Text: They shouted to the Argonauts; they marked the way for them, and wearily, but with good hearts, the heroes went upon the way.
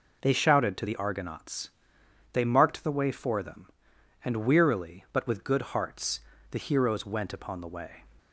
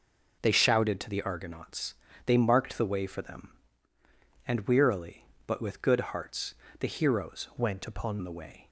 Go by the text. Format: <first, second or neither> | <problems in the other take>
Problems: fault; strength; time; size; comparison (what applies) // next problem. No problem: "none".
first | changes voice from "went" to "upon"; from 7.5 to 8.1 s; 0.6 s long